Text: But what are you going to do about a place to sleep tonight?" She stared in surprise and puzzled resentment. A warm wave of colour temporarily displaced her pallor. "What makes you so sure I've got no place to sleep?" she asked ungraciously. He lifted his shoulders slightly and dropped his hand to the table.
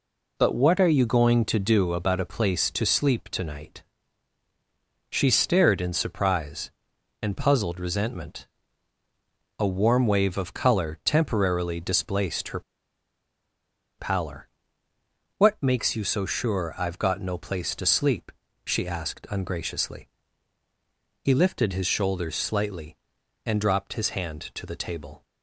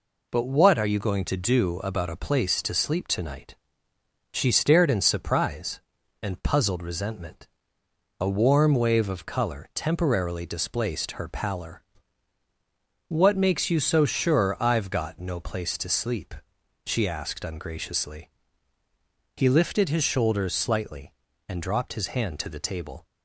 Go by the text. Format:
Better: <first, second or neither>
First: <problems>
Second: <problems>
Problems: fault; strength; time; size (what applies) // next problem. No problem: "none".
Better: second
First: pauses between "her" and "pallor"; strong; at 12.5 s; 1.3 s long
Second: none